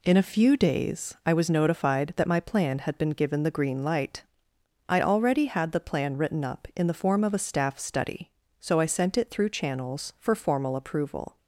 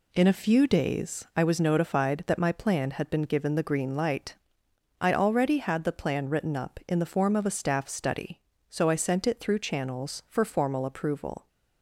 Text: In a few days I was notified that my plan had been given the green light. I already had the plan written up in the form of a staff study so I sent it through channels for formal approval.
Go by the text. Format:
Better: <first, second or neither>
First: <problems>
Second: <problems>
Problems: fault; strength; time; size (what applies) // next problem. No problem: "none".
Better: neither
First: none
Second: none